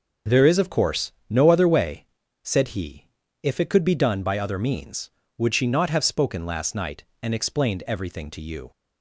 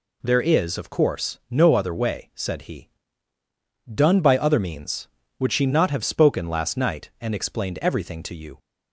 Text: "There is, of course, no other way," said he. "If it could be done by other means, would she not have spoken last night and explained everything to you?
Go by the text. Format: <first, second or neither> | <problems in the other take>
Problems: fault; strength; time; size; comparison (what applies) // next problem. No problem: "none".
first | skips "If it could be"; at 3.4 s